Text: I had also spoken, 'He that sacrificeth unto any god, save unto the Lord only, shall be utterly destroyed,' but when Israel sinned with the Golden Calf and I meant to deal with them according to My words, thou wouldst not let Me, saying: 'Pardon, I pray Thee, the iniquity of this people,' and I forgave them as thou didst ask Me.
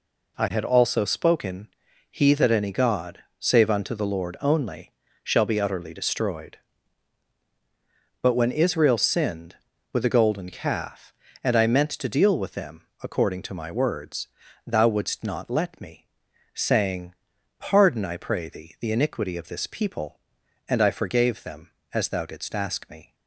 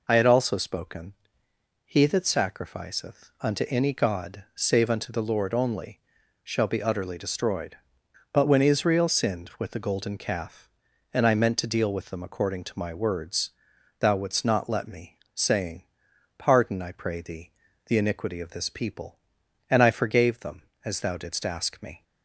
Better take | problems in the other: second | skips "sacrificeth unto"; at 2.5 s // pauses between "them" and "according"; slight; at 12.8 s; 0.16 s long

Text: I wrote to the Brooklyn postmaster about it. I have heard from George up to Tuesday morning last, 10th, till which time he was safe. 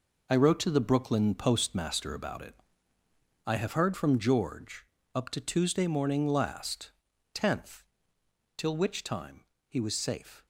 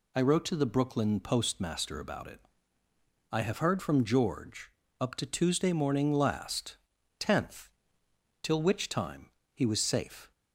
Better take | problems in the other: second | gets quieter; strong; throughout; 9.5 dB // pauses between "George" and "up"; slight; at 4.8 s; 0.28 s long; slight in the second // pauses between "time" and "he"; slight; at 9.4 s; 0.24 s long; slight in the second

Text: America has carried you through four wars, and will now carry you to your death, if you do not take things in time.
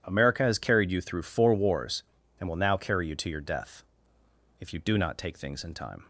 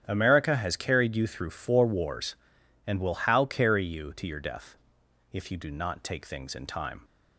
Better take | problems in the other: first | starts louder than the rest; strong; until 1.0 s; 9 dB // says "how" for "now"; at 3.1 s

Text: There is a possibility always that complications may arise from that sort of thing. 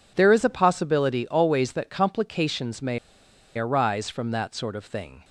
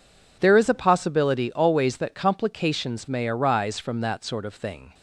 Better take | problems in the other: second | pauses between "may" and "arise"; noticeable; at 2.9 s; 0.59 s long

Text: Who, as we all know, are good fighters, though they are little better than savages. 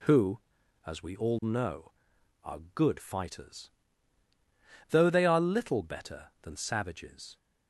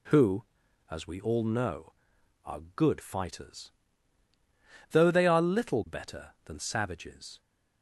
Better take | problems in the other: neither | pauses between "are" and "good"; slight; the same in both

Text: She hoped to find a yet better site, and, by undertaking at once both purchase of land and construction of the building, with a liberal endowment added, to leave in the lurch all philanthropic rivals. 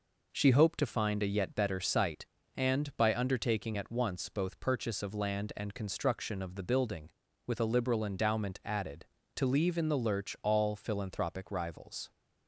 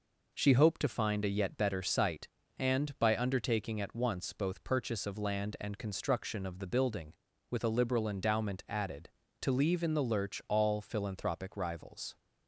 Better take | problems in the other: neither | none

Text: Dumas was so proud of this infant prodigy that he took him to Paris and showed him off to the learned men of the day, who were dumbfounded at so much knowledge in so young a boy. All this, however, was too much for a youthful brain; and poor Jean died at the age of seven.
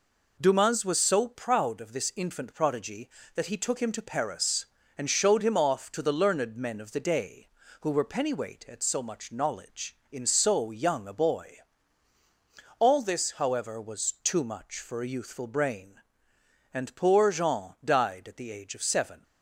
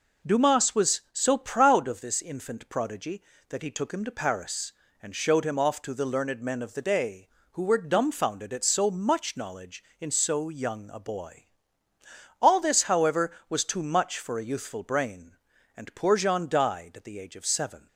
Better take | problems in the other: second | says "pennyweight" for "dumbfounded"; at 8.0 s

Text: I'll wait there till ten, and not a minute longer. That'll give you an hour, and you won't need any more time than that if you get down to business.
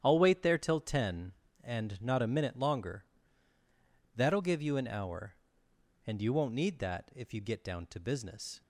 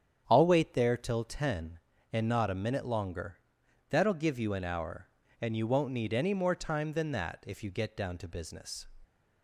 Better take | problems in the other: second | starts louder than the rest; strong; until 1.0 s; 9.5 dB; strong in the second // skips "any more time than"; at 6.7 s

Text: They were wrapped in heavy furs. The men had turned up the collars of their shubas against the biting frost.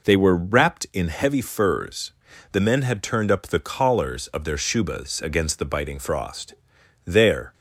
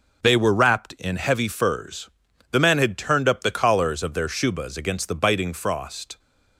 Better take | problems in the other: second | goes on to say "There"; slight; from 7.0 s on; 0.48 s long

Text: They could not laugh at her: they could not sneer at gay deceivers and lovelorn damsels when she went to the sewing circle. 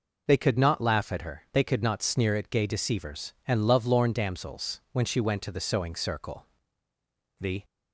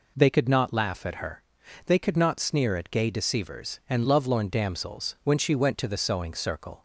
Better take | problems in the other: second | goes on to say "The"; slight; from 7.4 s on; 0.24 s long

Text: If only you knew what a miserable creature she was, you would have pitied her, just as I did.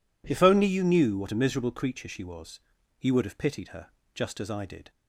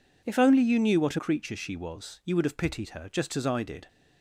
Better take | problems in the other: first | skips "miserable"; at 1.1 s

